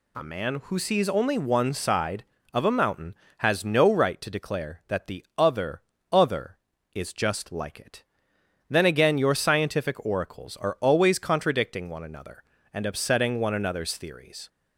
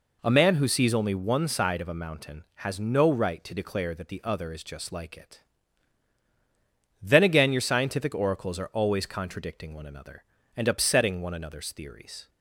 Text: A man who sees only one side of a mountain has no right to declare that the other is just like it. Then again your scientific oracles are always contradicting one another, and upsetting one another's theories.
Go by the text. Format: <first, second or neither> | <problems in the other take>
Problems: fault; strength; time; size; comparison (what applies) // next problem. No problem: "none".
second | says "other" twice; at 6.0 s